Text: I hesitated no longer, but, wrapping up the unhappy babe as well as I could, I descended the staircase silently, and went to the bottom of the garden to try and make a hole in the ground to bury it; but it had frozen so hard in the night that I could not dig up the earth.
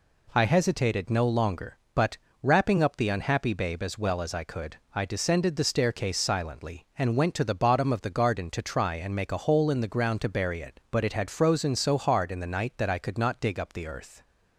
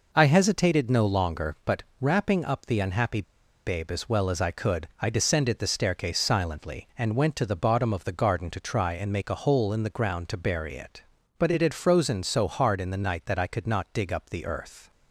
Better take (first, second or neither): first